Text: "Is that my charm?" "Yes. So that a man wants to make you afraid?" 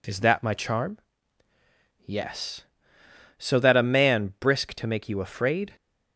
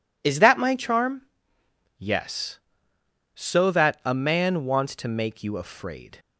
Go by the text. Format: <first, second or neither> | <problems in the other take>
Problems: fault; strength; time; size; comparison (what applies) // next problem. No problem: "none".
second | says "brisk" for "wants"; at 4.3 s